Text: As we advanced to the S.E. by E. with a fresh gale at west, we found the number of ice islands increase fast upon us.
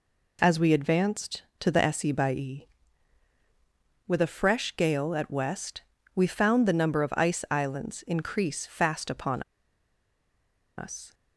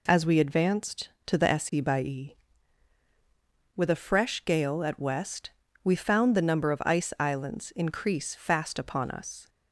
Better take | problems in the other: second | pauses between "upon" and "us"; strong; at 9.4 s; 1.3 s long

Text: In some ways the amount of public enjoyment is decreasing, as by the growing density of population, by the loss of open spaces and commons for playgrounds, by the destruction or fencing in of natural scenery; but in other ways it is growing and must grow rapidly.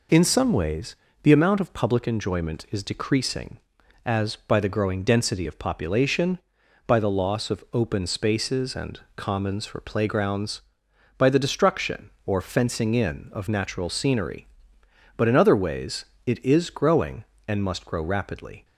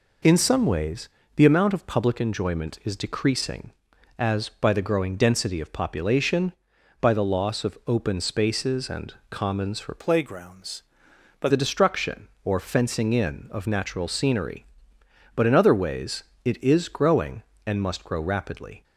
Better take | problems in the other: first | pauses between "ways" and "the"; slight; at 1.0 s; 0.26 s long; slight in the first // pauses between "and" and "commons"; slight; at 9.1 s; 0.16 s long; slight in the first // changes voice from "playgrounds" to "by"; from 9.9 to 11.4 s; 1.5 s long // pauses between "ways" and "it"; slight; at 16.2 s; 0.20 s long; slight in the first

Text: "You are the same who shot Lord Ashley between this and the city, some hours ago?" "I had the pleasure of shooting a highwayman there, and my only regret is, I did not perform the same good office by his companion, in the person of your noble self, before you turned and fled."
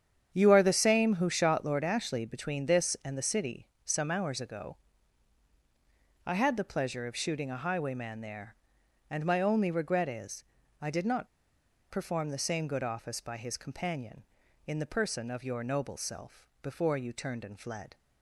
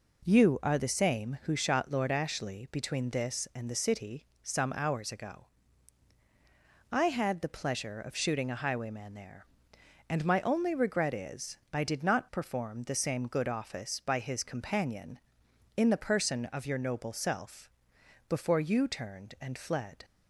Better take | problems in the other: second | starts louder than the rest; strong; until 1.3 s; 8.5 dB // pauses between "not" and "perform"; noticeable; at 11.2 s; 0.64 s long

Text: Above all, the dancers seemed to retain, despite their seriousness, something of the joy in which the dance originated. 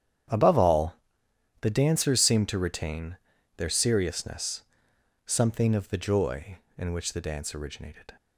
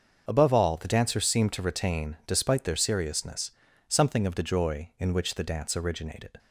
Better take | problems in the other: second | starts louder than the rest; strong; until 1.9 s; 9.5 dB; also in the second // skips "despite"; at 3.3 s

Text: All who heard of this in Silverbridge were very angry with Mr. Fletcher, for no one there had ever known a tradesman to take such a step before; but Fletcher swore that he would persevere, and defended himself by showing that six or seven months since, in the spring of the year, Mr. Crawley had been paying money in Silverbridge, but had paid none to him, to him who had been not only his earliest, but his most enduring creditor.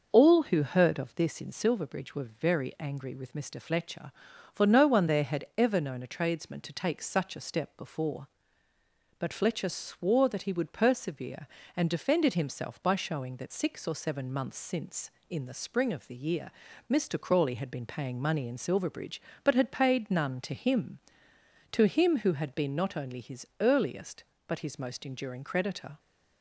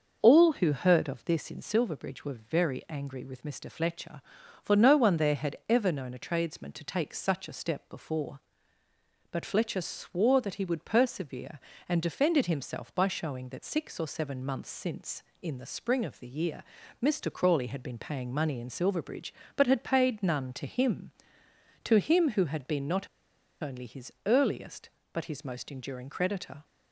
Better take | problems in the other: first | starts louder than the rest; noticeable; until 1.2 s; 6 dB; noticeable in the first // pauses between "not" and "only"; noticeable; at 23.0 s; 0.55 s long

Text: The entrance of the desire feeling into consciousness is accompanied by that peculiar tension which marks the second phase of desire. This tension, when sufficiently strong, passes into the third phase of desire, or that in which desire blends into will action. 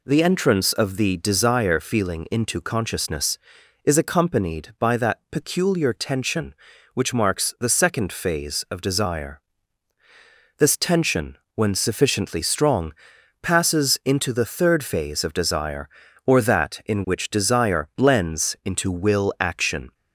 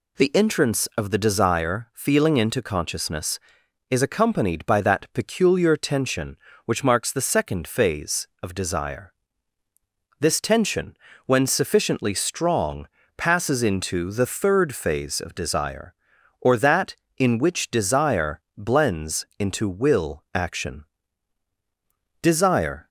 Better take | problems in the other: first | pauses between "desire" and "blends"; slight; at 18.3 s; 0.16 s long // goes on to say "Desire"; noticeable; from 22.2 s on; 0.66 s long

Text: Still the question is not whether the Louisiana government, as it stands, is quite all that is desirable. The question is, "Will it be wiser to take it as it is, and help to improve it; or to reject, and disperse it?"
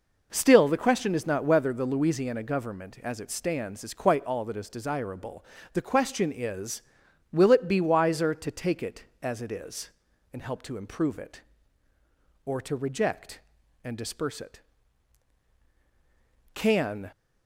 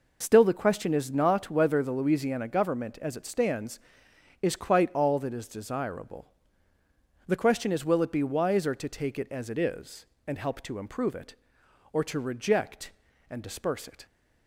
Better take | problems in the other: second | goes on to say "Can"; from 16.5 s on; 0.58 s long

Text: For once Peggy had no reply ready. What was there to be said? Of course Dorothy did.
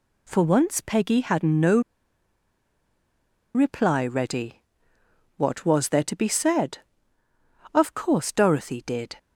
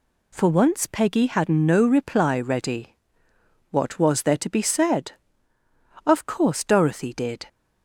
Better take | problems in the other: second | pauses between "no" and "reply"; strong; at 1.7 s; 1.7 s long

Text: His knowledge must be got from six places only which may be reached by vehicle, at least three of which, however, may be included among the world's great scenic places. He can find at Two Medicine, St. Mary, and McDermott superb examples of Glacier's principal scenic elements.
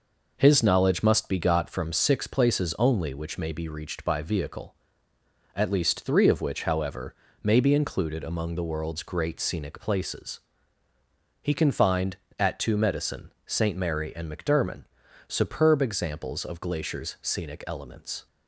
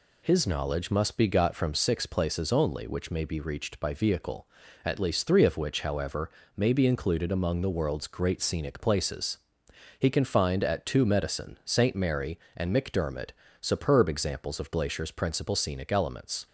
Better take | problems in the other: second | pauses between "McDermott" and "superb"; at 14.8 s; 0.42 s long; slight in the second // skips "principal"; at 17.1 s

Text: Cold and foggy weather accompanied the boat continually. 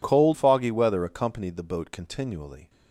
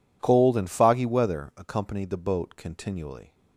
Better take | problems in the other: second | skips "and"; at 0.3 s

